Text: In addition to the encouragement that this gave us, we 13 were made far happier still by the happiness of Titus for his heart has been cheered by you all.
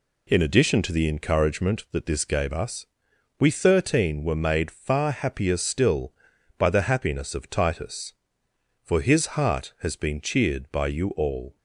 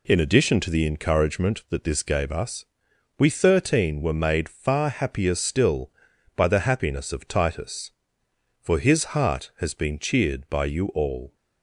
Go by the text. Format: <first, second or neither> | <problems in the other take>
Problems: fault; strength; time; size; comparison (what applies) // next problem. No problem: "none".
neither | none